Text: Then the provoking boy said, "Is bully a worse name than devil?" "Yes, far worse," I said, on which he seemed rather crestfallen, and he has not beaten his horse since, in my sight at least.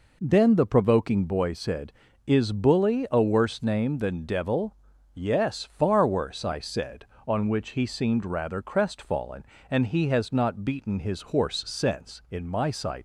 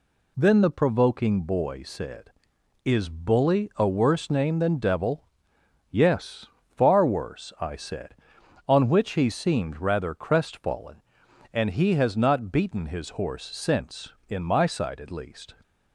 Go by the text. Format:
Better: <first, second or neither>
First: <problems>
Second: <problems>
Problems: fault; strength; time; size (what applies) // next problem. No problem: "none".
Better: second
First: stops before "at least"; at 12.9 s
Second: none